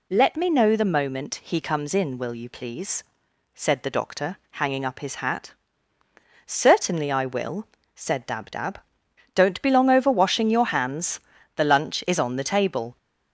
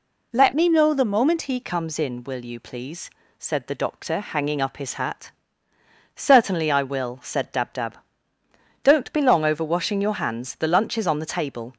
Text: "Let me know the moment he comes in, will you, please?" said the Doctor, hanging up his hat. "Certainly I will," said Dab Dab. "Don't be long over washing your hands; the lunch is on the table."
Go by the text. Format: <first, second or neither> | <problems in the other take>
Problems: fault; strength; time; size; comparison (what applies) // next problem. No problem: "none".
first | changes voice from "me" to "he"; from 0.5 to 1.5 s; 1.0 s long